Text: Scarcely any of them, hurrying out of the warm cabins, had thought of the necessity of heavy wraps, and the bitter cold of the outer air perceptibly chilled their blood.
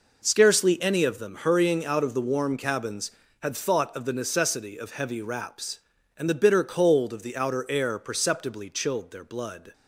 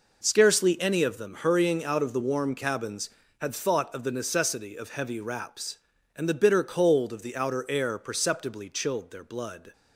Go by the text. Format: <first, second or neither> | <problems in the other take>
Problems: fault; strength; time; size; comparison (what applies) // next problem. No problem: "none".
neither | none